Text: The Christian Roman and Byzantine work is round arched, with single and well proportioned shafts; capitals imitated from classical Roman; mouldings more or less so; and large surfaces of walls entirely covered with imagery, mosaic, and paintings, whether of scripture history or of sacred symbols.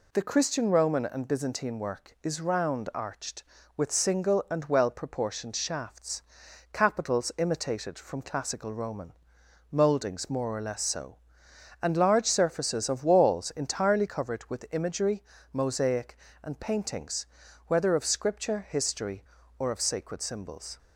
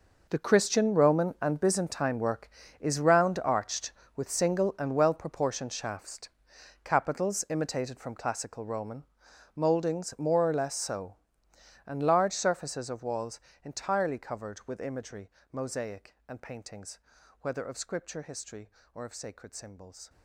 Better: first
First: none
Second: gets quieter; strong; throughout; 15 dB // pauses between "walls" and "entirely"; slight; at 13.3 s; 0.24 s long

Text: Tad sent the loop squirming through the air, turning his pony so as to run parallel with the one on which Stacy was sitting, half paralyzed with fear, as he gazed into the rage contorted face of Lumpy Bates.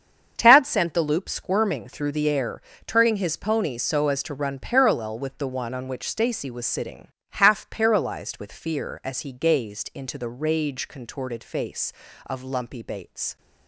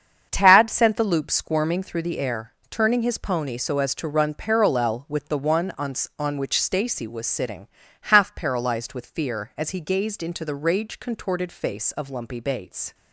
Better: first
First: starts louder than the rest; strong; until 1.3 s; 7.5 dB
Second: starts louder than the rest; strong; until 1.3 s; 7.5 dB // says "on" twice; at 6.1 s

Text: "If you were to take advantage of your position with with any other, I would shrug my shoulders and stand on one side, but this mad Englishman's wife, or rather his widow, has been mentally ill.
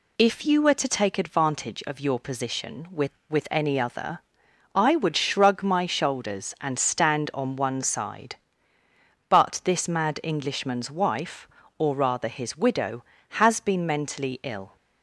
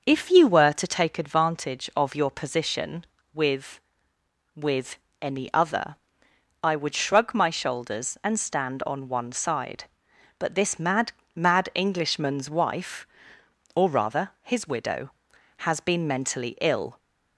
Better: first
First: none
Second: pauses between "with" and "any"; slight; at 4.9 s; 0.24 s long // says "mad" twice; at 11.3 s

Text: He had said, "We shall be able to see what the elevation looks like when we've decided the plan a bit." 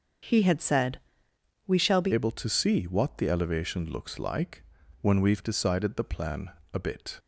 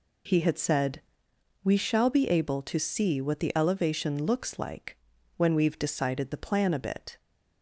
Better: second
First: starts louder than the rest; until 1.9 s; 6 dB // changes voice at "able"; from 2.1 s on; 5.0 s long // pauses between "like" and "when"; at 4.6 s; 0.38 s long // pauses between "plan" and "a"; slight; at 6.5 s; 0.22 s long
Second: pauses between "like" and "when"; at 4.9 s; 0.40 s long

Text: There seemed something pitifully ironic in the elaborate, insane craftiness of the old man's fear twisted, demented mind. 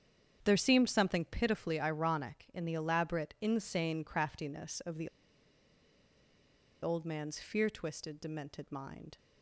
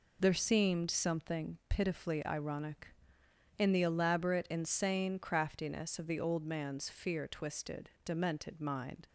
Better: second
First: starts louder than the rest; strong; until 1.4 s; 8.5 dB // pauses between "the" and "old"; strong; at 5.0 s; 1.7 s long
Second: none

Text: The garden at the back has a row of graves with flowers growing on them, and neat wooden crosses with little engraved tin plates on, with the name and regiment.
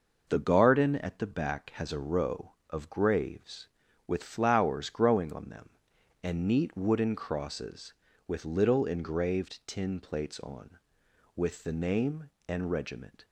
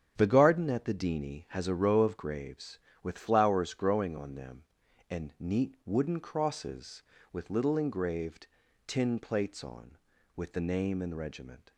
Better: first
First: none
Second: starts louder than the rest; strong; until 1.1 s; 8.5 dB // says "dini" for "back"; at 0.9 s // pauses between "engraved" and "tin"; at 8.4 s; 0.40 s long

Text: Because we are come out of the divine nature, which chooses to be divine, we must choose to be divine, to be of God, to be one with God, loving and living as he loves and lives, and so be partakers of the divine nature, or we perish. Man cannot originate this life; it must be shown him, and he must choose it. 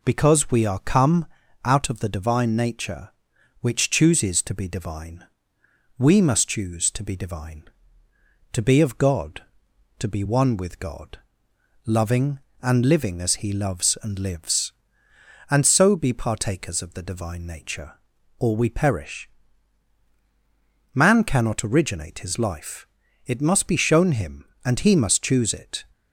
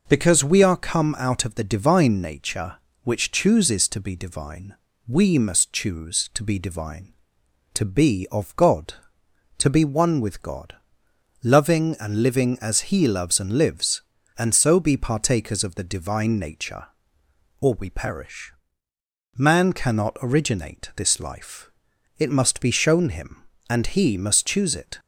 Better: second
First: pauses between "come" and "out"; slight; at 1.2 s; 0.36 s long // says "his" for "this"; at 22.2 s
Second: none

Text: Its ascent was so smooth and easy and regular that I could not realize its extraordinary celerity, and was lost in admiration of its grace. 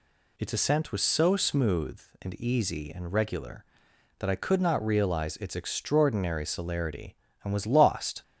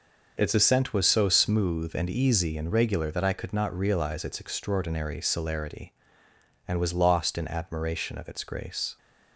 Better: second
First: stops before "in admiration of its grace"; at 8.2 s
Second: none

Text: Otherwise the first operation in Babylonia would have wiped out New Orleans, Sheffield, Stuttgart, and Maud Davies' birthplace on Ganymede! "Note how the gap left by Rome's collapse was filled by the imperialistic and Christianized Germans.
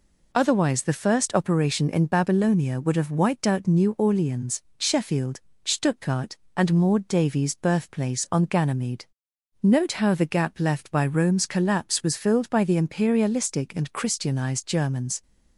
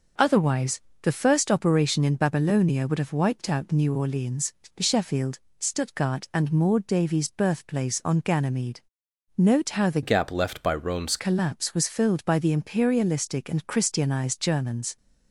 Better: first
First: none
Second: pauses between "Otherwise" and "the"; slight; at 0.8 s; 0.22 s long // changes voice from "gap" to "Rome's"; from 10.0 to 11.1 s; 1.1 s long

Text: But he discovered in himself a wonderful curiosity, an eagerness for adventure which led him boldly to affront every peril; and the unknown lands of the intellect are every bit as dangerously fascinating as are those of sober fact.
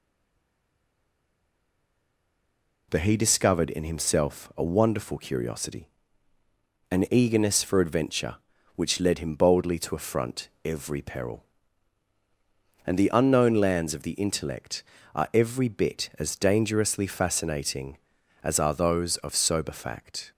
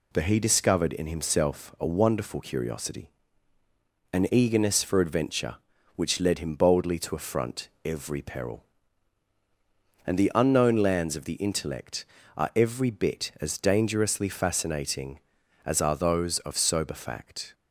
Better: second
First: stays silent before the first word; strong; until 2.8 s; 2.8 s long // pauses between "affront" and "every"; slight; at 10.4 s; 0.18 s long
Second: pauses between "affront" and "every"; slight; at 7.6 s; 0.18 s long

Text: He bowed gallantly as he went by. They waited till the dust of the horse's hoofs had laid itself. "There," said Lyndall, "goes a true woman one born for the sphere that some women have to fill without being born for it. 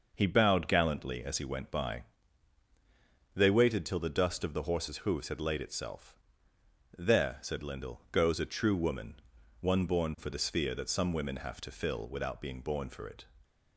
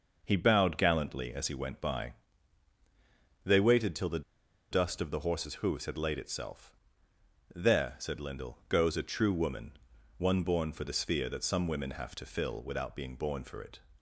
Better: first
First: pauses between "woman" and "one"; noticeable; at 9.1 s; 0.46 s long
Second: pauses between "the" and "dust"; noticeable; at 4.2 s; 0.50 s long // pauses between "woman" and "one"; noticeable; at 9.7 s; 0.46 s long

